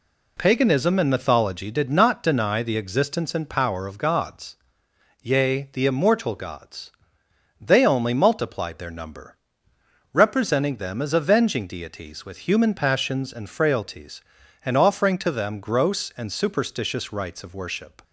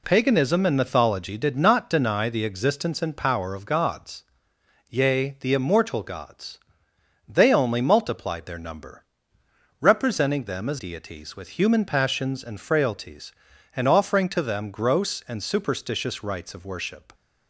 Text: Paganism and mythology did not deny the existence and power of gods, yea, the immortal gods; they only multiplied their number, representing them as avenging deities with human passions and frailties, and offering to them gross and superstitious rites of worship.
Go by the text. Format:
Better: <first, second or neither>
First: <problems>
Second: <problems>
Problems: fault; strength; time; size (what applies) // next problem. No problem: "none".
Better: first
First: none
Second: skips "avenging"; at 10.7 s